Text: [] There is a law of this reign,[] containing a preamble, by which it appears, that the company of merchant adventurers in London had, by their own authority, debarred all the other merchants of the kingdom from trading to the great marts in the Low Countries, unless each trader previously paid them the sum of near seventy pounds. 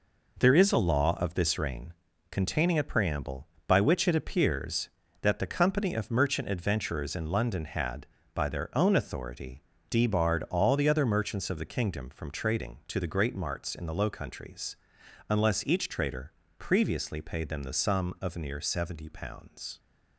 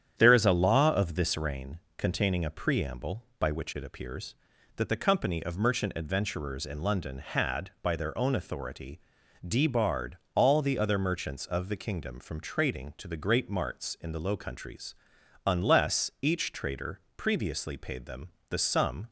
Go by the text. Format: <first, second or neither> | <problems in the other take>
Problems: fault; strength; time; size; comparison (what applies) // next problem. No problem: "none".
first | starts louder than the rest; strong; until 1.1 s; 9.5 dB // pauses between "debarred" and "all"; slight; at 10.1 s; 0.18 s long // pauses between "trader" and "previously"; slight; at 16.9 s; 0.16 s long; slight in the first // pauses between "them" and "the"; slight; at 18.2 s; 0.22 s long // stops before "of near seventy pounds"; at 19.0 s